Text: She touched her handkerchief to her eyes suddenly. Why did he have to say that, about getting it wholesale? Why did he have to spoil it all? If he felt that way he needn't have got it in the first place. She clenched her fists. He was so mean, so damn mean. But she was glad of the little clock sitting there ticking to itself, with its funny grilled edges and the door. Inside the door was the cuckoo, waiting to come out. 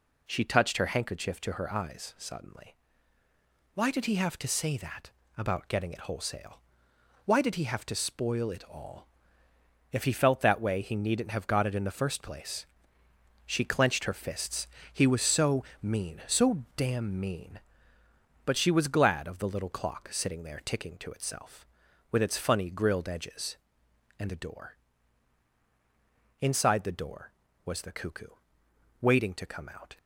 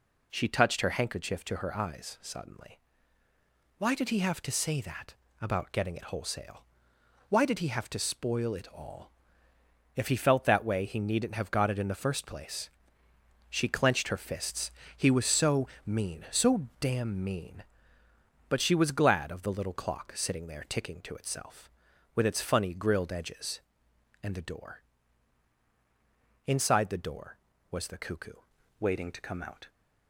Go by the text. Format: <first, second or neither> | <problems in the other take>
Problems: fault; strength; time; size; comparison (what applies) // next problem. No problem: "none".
first | pauses between "so" and "mean"; slight; at 15.6 s; 0.18 s long; slight in the first // changes voice at "waiting"; from 28.7 s on; 0.9 s long